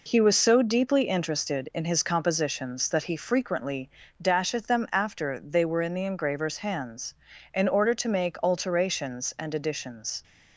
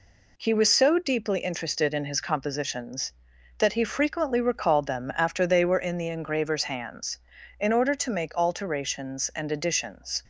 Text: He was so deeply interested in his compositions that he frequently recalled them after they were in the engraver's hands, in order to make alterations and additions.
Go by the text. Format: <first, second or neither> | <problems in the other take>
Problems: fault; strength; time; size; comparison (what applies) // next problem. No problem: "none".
second | says "dasheth" for "recalled"; at 4.2 s